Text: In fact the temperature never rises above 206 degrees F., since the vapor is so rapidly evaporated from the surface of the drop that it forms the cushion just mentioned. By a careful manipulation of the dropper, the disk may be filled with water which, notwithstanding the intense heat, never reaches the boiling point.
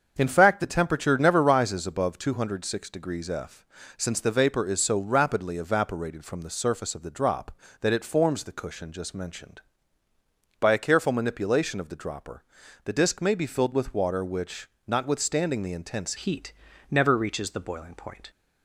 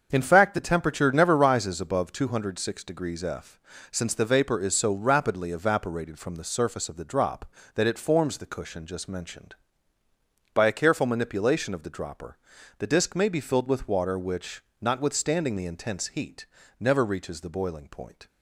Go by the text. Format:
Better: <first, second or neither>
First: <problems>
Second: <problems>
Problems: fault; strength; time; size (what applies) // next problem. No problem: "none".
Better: second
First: starts louder than the rest; until 1.1 s; 7 dB // changes voice at "heat"; from 16.1 s on; 2.1 s long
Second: starts louder than the rest; until 1.1 s; 7 dB